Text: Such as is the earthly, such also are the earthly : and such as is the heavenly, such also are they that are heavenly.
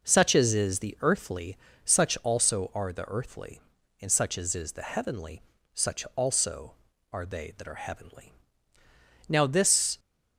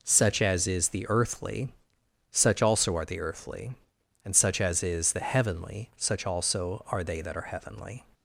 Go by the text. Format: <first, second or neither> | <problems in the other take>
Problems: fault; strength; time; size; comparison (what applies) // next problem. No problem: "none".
second | goes on to say "Now this"; noticeable; from 9.2 s on; 0.70 s long